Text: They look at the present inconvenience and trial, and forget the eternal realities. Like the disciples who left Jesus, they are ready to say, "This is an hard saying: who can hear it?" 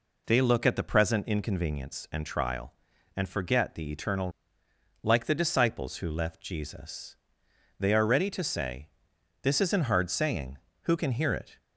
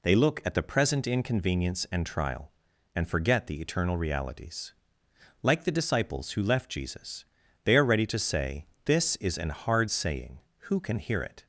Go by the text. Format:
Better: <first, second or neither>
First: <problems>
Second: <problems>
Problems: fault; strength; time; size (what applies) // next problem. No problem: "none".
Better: second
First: skips "realities"; at 4.6 s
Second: none